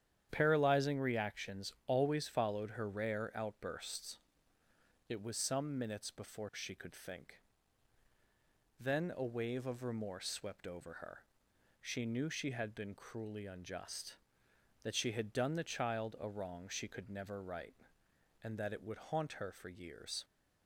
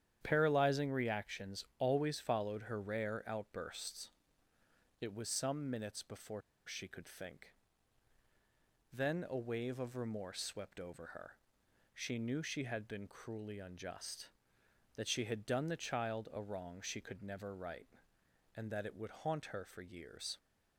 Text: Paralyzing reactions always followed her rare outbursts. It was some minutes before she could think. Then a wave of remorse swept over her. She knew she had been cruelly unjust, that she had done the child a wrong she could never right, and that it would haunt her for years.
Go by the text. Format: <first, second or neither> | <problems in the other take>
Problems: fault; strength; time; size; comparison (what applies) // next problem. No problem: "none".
first | starts louder than the rest; strong; until 1.2 s; 9.5 dB; strong in the first // pauses between "reactions" and "always"; slight; at 1.6 s; 0.16 s long; slight in the first // pauses between "before" and "she"; slight; at 6.4 s; 0.25 s long